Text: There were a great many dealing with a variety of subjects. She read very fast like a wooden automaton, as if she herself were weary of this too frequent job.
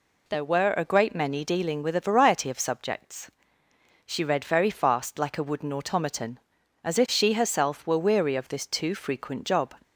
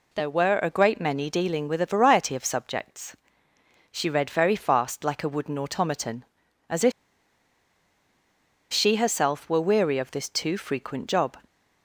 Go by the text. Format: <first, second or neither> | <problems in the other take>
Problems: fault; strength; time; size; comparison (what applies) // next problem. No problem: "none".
first | pauses between "if" and "she"; strong; at 6.9 s; 1.8 s long